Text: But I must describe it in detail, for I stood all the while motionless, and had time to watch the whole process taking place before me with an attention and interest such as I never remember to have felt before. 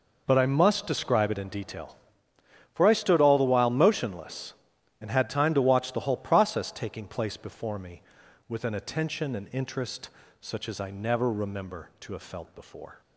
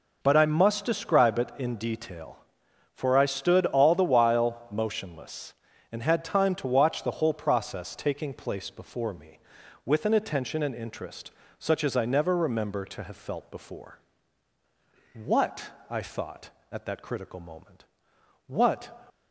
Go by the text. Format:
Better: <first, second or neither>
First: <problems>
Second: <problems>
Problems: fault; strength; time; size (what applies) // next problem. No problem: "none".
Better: first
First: pauses between "interest" and "such"; slight; at 10.0 s; 0.32 s long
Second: pauses between "interest" and "such"; slight; at 11.3 s; 0.28 s long // goes on to say "What I thought at that critical moment what"; strong; from 15.1 s on; 3.8 s long